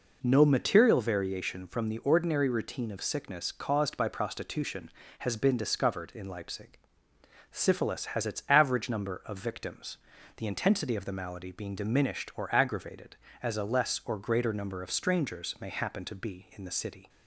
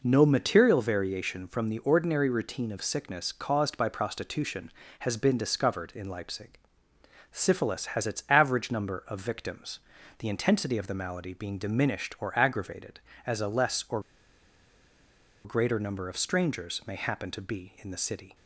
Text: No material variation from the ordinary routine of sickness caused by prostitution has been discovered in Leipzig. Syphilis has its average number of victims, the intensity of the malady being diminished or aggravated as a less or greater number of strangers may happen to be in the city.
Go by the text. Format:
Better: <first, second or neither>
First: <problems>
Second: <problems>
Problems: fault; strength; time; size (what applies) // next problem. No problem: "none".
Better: first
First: none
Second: pauses between "or" and "greater"; strong; at 14.0 s; 1.4 s long